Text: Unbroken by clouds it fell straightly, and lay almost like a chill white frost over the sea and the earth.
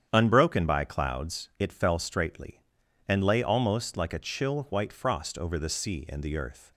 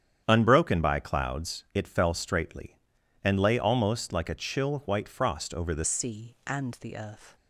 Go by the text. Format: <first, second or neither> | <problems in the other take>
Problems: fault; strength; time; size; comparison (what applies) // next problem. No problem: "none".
first | starts louder than the rest; strong; until 1.2 s; 8.5 dB; strong in the first // changes voice at "sea"; from 5.8 s on; 1.5 s long